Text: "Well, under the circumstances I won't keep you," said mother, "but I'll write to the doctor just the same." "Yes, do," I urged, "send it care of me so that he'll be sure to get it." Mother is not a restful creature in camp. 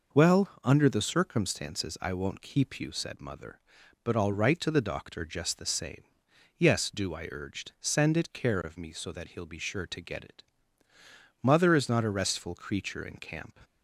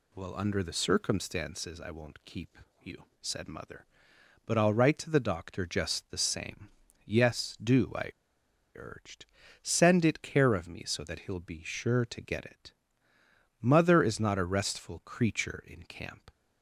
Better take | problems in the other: first | pauses between "keep" and "you"; slight; at 2.5 s; 0.24 s long // pauses between "I" and "urged"; noticeable; at 8.1 s; 0.64 s long

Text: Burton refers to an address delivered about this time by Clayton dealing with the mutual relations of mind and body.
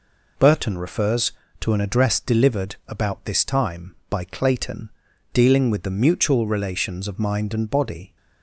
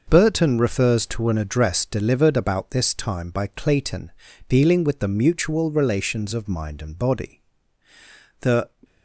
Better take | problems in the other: first | pauses between "Clayton" and "dealing"; at 4.1 s; 0.38 s long; also in the first // goes on to say "The"; slight; from 8.4 s on; 0.28 s long

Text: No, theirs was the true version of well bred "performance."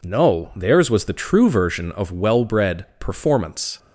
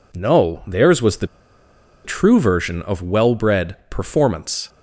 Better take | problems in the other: first | pauses between "the" and "true"; noticeable; at 1.2 s; 0.78 s long

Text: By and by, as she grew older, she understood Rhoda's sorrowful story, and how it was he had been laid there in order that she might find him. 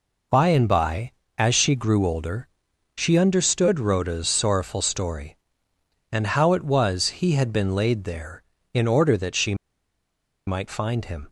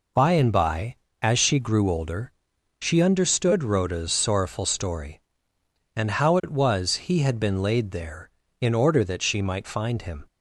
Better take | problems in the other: second | pauses between "she" and "might"; noticeable; at 9.5 s; 0.91 s long

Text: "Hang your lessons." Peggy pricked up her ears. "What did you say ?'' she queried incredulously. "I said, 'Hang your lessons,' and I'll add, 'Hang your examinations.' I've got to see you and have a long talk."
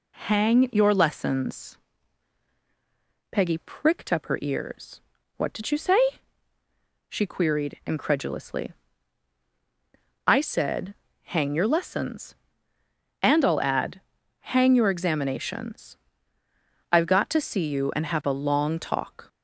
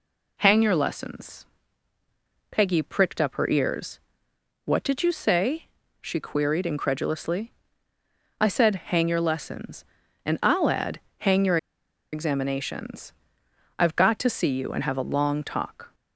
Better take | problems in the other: first | pauses between "your" and "examinations"; noticeable; at 11.5 s; 0.55 s long

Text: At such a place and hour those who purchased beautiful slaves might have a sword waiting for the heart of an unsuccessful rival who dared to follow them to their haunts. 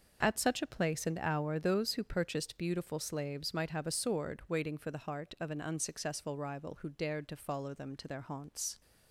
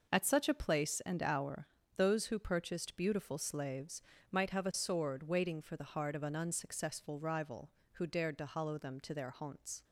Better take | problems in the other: first | pauses between "hour" and "those"; slight; at 1.6 s; 0.30 s long // pauses between "slaves" and "might"; slight; at 4.0 s; 0.30 s long // says "hollow" for "follow"; at 8.4 s

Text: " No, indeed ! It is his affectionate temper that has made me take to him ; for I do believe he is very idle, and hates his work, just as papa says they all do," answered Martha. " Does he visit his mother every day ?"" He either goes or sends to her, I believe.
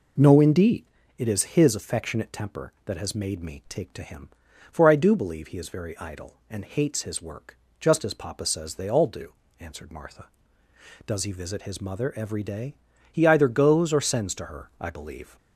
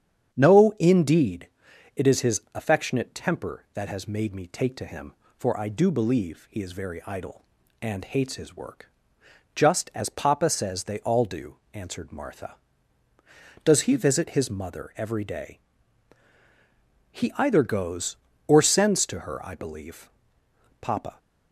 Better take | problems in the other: first | starts louder than the rest; strong; until 1.3 s; 8 dB // goes on to say "Papa"; slight; from 20.8 s on; 0.38 s long

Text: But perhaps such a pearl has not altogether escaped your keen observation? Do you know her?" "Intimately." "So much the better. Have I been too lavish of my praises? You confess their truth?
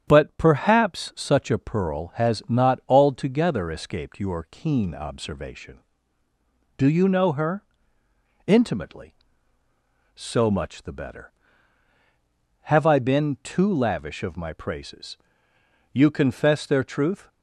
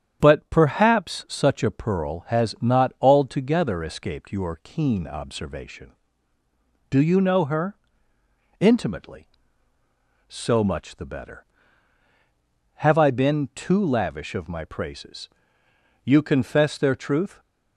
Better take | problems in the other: neither | starts louder than the rest; strong; the same in both

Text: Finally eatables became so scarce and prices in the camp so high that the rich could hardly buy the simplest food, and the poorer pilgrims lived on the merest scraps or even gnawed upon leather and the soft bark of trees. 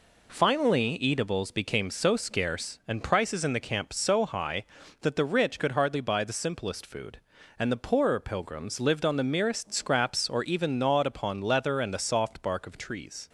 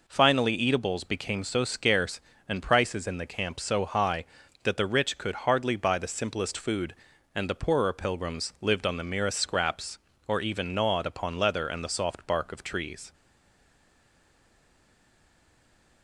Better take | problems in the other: first | stays silent after the last word; strong; from 13.1 s on; 2.9 s long

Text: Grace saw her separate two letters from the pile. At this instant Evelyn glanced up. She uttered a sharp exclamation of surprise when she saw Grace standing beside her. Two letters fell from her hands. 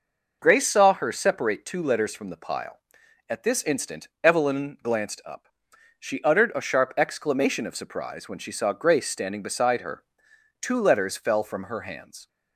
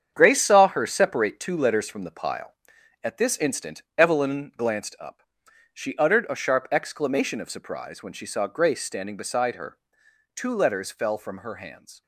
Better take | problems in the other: first | gets quieter; strong; throughout; 8.5 dB

